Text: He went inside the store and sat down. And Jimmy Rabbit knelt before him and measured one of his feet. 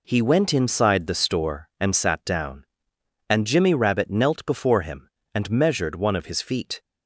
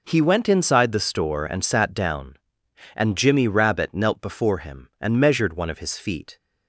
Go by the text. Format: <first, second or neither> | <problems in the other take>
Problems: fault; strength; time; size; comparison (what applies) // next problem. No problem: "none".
neither | none